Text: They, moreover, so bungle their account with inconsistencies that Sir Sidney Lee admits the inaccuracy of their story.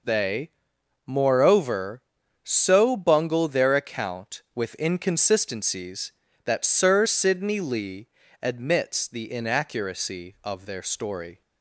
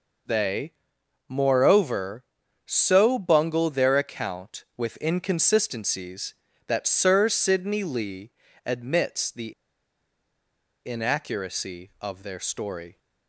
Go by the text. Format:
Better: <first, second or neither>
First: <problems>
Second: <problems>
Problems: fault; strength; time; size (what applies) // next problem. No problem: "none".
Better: first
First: pauses between "Lee" and "admits"; slight; at 8.0 s; 0.34 s long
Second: pauses between "Lee" and "admits"; slight; at 8.3 s; 0.34 s long // pauses between "the" and "inaccuracy"; strong; at 9.5 s; 1.3 s long